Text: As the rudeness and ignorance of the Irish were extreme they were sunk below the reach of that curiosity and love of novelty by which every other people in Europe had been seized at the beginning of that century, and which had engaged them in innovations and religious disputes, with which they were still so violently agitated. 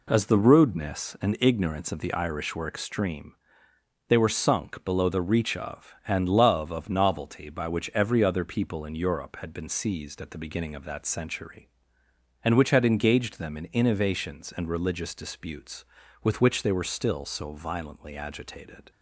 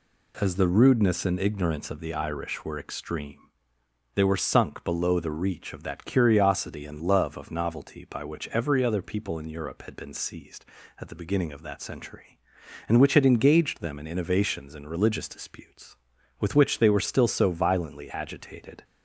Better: second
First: pauses between "extreme" and "they"; noticeable; at 3.3 s; 0.74 s long // skips "that curiosity"; at 6.0 s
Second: pauses between "extreme" and "they"; noticeable; at 3.3 s; 0.78 s long

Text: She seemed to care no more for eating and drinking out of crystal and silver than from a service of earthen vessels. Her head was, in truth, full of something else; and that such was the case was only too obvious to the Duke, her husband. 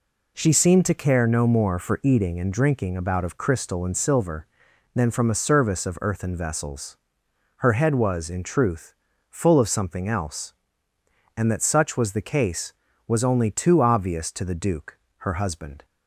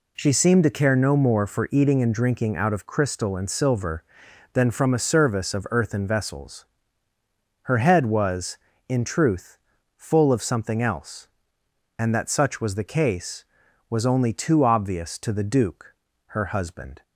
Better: second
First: says "about" for "out"; at 2.9 s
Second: none

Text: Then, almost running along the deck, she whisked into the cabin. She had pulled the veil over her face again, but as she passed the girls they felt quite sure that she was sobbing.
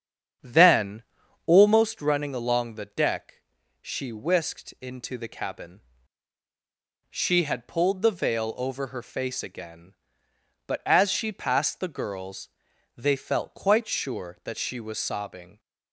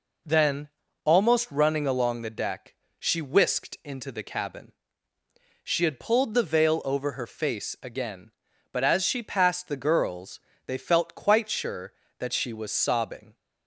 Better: second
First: starts louder than the rest; strong; until 1.9 s; 8 dB // pauses between "girls" and "they"; noticeable; at 12.4 s; 0.48 s long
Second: pauses between "girls" and "they"; slight; at 10.4 s; 0.26 s long

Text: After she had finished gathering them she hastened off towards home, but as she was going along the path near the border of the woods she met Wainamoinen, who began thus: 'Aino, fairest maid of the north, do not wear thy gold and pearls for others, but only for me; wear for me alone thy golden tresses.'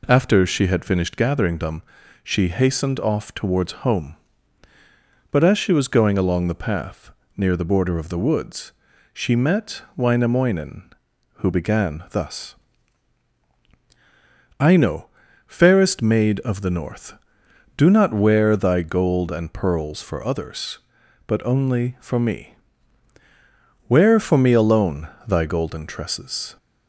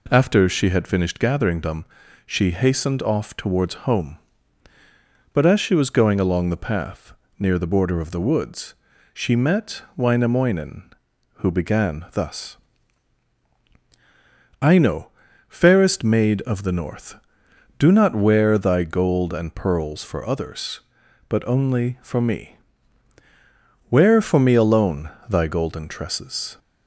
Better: neither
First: pauses between "them" and "she"; at 1.8 s; 0.40 s long // pauses between "path" and "near"; slight; at 7.1 s; 0.26 s long // pauses between "woods" and "she"; at 8.7 s; 0.42 s long // pauses between "met" and "Wainamoinen"; slight; at 9.8 s; 0.16 s long // pauses between "alone" and "thy"; slight; at 25.0 s; 0.22 s long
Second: pauses between "them" and "she"; at 1.8 s; 0.40 s long // pauses between "path" and "near"; slight; at 7.1 s; 0.26 s long // pauses between "woods" and "she"; at 8.7 s; 0.40 s long // pauses between "met" and "Wainamoinen"; slight; at 9.8 s; 0.16 s long // pauses between "alone" and "thy"; slight; at 25.0 s; 0.22 s long

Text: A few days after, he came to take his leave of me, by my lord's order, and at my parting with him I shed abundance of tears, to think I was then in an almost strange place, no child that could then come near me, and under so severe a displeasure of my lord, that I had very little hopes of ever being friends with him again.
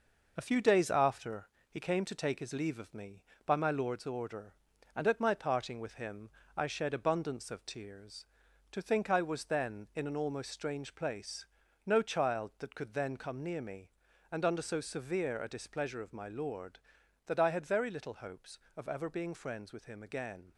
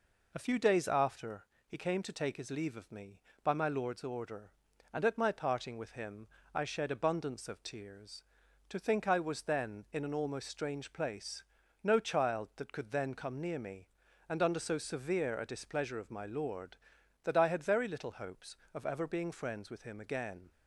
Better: second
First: gets quieter; noticeable; throughout; 5 dB // pauses between "him" and "I"; slight; at 6.2 s; 0.26 s long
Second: pauses between "him" and "I"; slight; at 6.2 s; 0.26 s long

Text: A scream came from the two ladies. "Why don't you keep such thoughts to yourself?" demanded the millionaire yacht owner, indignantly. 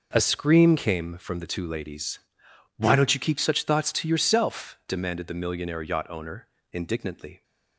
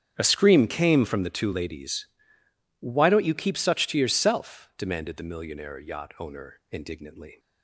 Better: first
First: none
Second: starts louder than the rest; strong; until 1.1 s; 8.5 dB // skips "thoughts"; at 3.8 s

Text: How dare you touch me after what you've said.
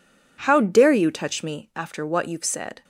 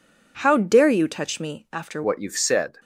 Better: first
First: none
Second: changes voice at "what"; from 2.0 s on; 0.7 s long

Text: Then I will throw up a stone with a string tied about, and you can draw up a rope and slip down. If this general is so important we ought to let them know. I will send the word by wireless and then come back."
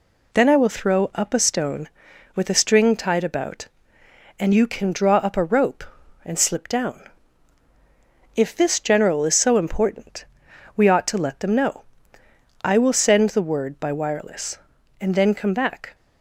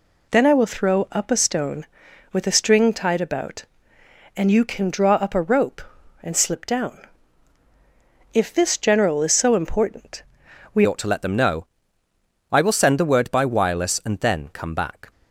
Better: first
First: pauses between "important" and "we"; noticeable; at 10.2 s; 0.52 s long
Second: pauses between "important" and "we"; noticeable; at 10.2 s; 0.52 s long // changes voice at "ought"; from 10.8 s on; 4.3 s long

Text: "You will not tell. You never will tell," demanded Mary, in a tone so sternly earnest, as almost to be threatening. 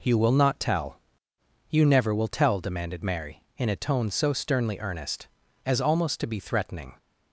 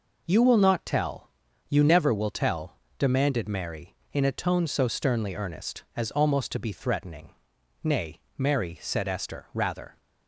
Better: first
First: none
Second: goes on to say "Nay Mary said Esther rather"; strong; from 7.8 s on; 2.1 s long

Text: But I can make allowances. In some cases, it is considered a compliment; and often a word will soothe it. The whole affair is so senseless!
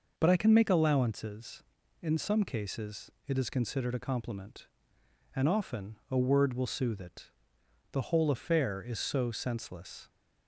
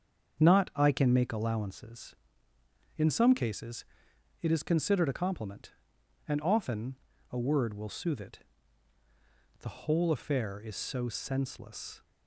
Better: first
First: none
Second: starts louder than the rest; until 1.4 s; 7 dB // says "Not" for "But"; at 0.4 s // pauses between "often" and "a"; at 6.9 s; 0.38 s long

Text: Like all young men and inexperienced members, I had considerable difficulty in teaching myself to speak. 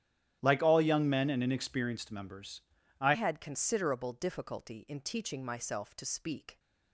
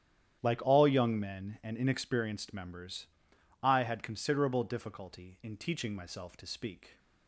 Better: second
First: starts louder than the rest; strong; until 1.4 s; 11 dB // changes voice at "had"; from 3.1 s on; 3.4 s long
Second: starts louder than the rest; strong; until 1.4 s; 10.5 dB

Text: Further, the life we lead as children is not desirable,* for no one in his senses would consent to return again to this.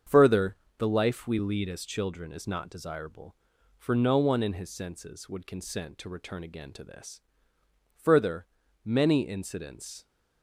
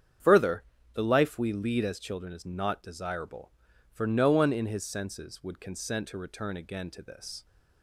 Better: second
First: starts louder than the rest; until 1.3 s; 7 dB // goes on to say "Further many incidents"; strong; from 8.0 s on; 2.0 s long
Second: starts louder than the rest; strong; until 1.5 s; 8 dB

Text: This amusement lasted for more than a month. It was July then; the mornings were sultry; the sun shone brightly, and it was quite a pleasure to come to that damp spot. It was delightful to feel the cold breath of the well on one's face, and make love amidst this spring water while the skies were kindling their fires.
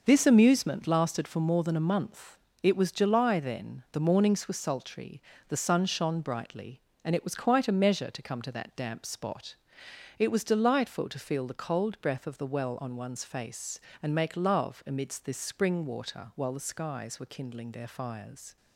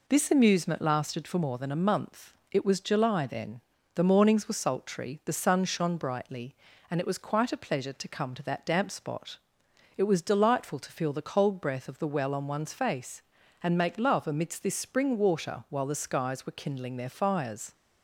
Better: second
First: starts louder than the rest; noticeable; until 1.0 s; 6 dB // says "measure" for "pleasure"; at 7.7 s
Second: none

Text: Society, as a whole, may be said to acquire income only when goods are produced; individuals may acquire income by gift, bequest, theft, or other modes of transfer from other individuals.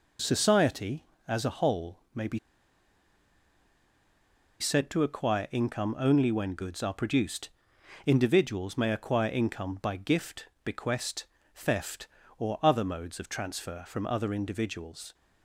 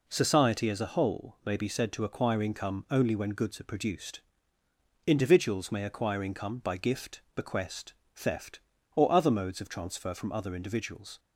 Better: second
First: pauses between "be" and "said"; strong; at 2.3 s; 2.2 s long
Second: none

